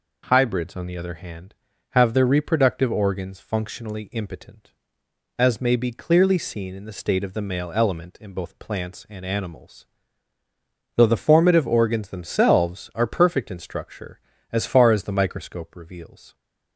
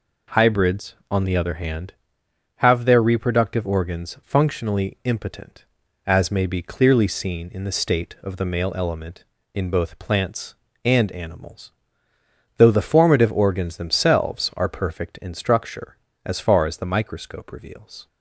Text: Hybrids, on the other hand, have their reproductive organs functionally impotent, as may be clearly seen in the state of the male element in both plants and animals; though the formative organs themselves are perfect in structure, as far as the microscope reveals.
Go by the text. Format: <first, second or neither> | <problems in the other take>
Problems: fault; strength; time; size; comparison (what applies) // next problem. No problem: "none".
neither | none